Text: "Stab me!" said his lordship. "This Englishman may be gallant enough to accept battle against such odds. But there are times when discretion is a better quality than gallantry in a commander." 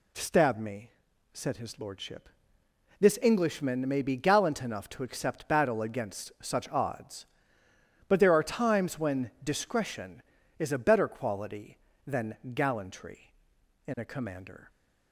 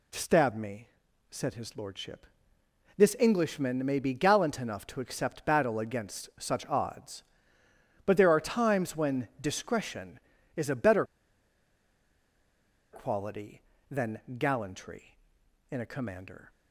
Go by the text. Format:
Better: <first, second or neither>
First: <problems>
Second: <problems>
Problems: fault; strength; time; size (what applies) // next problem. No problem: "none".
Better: first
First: pauses between "than" and "gallantry"; slight; at 12.3 s; 0.18 s long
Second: pauses between "better" and "quality"; strong; at 11.0 s; 1.8 s long // pauses between "than" and "gallantry"; slight; at 14.2 s; 0.18 s long